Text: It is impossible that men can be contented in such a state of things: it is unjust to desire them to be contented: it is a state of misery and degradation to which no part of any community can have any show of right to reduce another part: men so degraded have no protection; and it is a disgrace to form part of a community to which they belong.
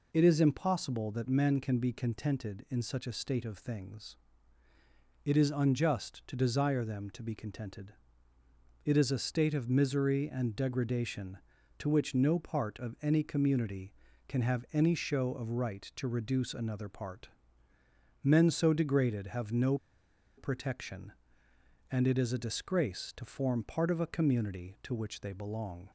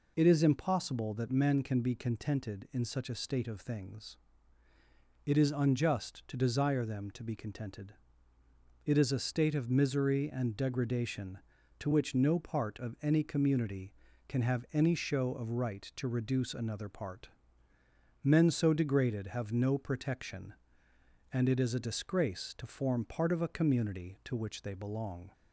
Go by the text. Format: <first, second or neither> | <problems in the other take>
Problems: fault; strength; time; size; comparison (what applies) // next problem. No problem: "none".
second | pauses between "no" and "protection"; noticeable; at 19.7 s; 0.61 s long